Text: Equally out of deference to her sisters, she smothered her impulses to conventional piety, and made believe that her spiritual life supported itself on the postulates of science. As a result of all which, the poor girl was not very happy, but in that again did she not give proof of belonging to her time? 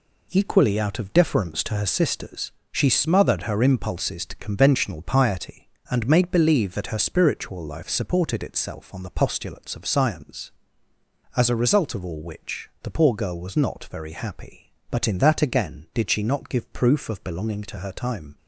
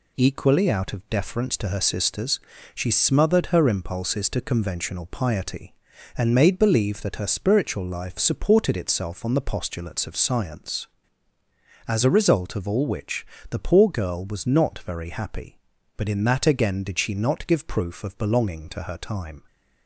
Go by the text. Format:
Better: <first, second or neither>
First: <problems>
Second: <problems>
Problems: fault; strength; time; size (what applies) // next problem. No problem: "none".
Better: neither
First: none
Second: none